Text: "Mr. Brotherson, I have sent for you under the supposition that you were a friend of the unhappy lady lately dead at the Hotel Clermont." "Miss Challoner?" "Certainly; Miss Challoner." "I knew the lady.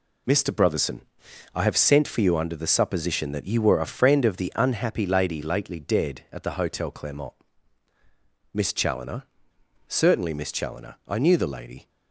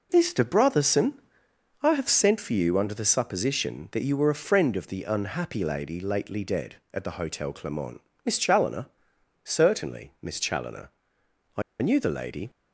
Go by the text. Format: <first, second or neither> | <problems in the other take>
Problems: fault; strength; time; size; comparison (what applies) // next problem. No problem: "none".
first | pauses between "I" and "knew"; slight; at 11.6 s; 0.19 s long